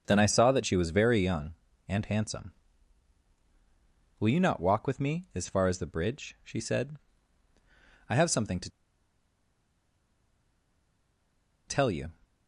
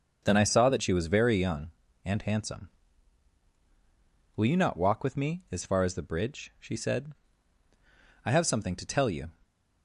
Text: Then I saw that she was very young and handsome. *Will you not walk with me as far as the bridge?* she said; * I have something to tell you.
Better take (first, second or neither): second